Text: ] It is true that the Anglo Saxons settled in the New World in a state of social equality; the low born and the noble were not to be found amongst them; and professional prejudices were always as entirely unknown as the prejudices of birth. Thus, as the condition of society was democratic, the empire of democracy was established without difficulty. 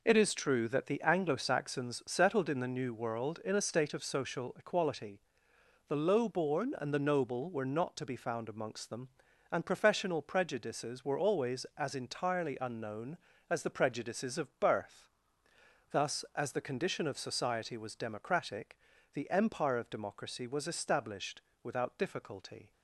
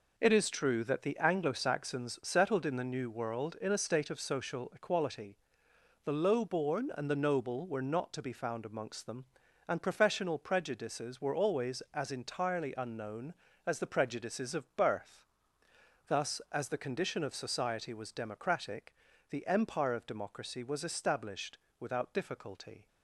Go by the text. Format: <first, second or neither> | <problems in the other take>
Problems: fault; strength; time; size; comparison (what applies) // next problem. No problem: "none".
neither | pauses between "established" and "without"; slight; the same in both